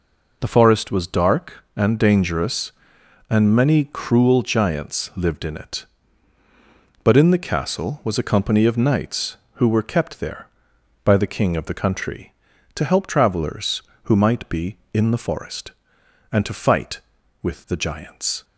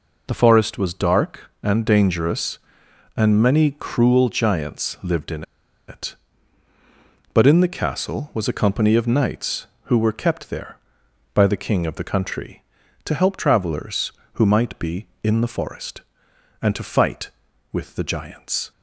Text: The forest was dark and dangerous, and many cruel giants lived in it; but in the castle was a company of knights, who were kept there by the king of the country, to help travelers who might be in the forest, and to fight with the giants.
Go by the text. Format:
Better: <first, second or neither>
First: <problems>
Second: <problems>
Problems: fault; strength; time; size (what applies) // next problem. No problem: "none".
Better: first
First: none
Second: pauses between "in" and "it"; noticeable; at 5.4 s; 0.46 s long